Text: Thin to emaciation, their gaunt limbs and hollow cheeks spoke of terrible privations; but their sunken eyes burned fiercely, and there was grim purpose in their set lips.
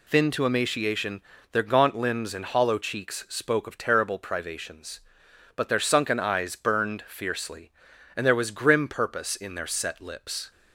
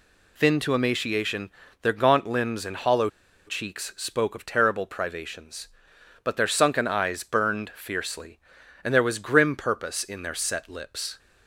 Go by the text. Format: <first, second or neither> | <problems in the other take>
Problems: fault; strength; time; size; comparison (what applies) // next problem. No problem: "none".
first | pauses between "hollow" and "cheeks"; at 3.0 s; 0.39 s long